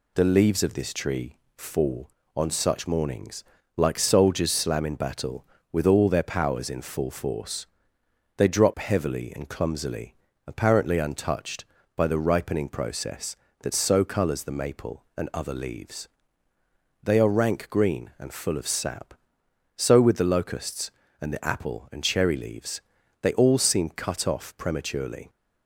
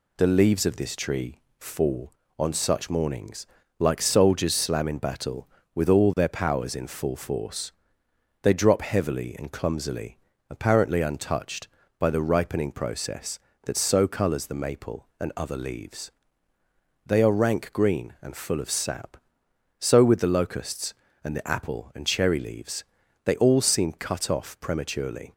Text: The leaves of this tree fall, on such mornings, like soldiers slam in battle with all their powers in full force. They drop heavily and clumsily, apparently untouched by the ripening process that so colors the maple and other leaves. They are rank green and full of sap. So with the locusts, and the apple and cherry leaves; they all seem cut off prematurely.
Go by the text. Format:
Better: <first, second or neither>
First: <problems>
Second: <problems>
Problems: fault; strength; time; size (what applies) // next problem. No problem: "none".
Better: neither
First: pauses between "tree" and "fall"; slight; at 1.3 s; 0.18 s long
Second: pauses between "tree" and "fall"; slight; at 1.3 s; 0.18 s long